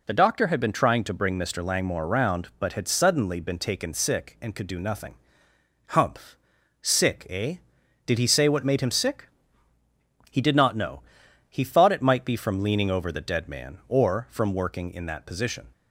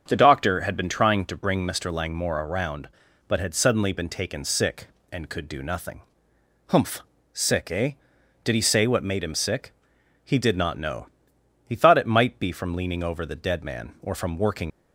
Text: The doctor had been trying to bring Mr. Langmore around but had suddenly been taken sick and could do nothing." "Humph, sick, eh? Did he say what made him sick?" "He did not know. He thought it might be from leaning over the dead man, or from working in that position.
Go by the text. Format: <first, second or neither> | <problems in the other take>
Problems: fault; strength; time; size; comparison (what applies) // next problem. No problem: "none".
first | starts louder than the rest; until 1.0 s; 7 dB // stops before "in that position"; at 14.6 s